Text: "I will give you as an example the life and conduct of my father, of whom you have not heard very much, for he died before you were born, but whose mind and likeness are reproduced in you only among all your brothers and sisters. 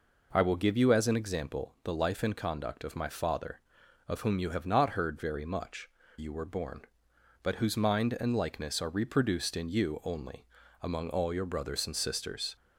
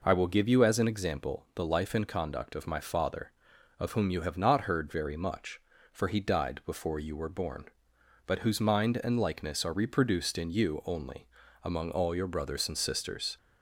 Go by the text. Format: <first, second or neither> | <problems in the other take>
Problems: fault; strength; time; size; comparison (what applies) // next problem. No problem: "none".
second | skips "for he died before"; at 6.0 s // pauses between "only" and "among"; slight; at 10.4 s; 0.36 s long; slight in the second